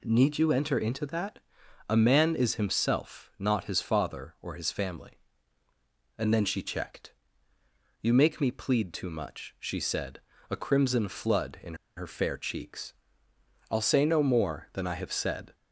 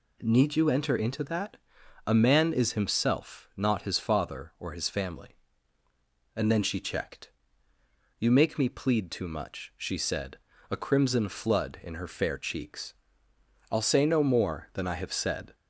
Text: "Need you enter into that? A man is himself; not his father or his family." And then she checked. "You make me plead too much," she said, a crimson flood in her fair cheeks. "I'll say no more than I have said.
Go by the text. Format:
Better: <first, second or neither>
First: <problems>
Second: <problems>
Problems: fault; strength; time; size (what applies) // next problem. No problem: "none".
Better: second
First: pauses between "in" and "her"; slight; at 11.7 s; 0.22 s long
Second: none